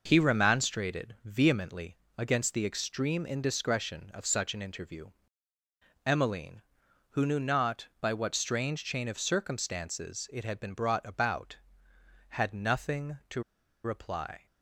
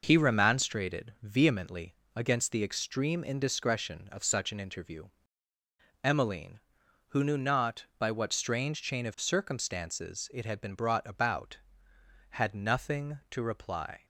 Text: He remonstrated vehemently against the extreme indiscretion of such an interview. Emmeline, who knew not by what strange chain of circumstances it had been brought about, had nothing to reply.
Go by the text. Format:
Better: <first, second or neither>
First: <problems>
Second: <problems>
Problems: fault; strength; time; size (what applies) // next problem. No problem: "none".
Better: second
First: pauses between "vehemently" and "against"; slight; at 1.9 s; 0.20 s long // pauses between "to" and "reply"; at 13.4 s; 0.43 s long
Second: pauses between "vehemently" and "against"; slight; at 1.9 s; 0.20 s long